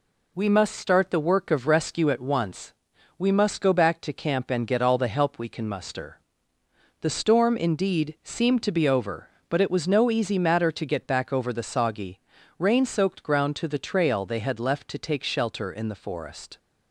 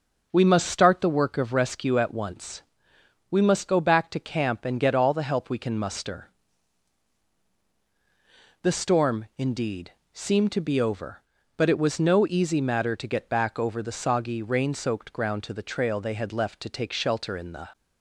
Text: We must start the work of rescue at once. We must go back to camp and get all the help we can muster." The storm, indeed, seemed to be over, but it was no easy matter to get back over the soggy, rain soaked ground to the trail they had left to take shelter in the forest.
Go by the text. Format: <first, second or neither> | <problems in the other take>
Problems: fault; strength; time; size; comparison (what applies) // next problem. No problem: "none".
first | starts louder than the rest; until 1.3 s; 6.5 dB // stops before "forest"; at 17.7 s